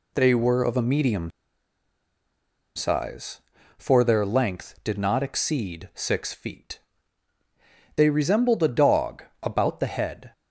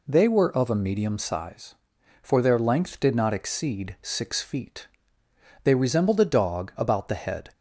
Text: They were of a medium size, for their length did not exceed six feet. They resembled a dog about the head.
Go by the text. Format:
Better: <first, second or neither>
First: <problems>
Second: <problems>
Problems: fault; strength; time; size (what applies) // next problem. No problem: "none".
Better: second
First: pauses between "medium" and "size"; strong; at 1.3 s; 1.4 s long // pauses between "dog" and "about"; slight; at 9.2 s; 0.18 s long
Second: none